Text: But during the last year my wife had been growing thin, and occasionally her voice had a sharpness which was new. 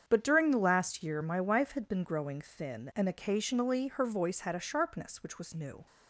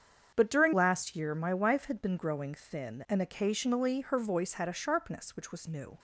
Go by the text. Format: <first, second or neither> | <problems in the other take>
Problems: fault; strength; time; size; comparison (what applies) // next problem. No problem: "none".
first | starts louder than the rest; strong; until 1.3 s; 7.5 dB; strong in the first // skips "the"; at 0.7 s